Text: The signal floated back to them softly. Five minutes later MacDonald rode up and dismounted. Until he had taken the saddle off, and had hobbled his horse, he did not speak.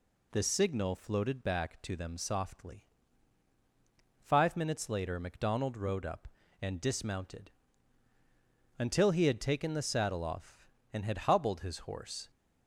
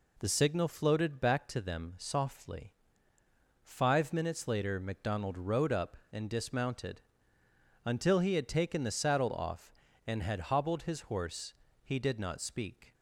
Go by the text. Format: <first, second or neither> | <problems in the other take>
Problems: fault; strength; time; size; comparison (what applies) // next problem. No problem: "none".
second | stops before "he did not speak"; at 12.2 s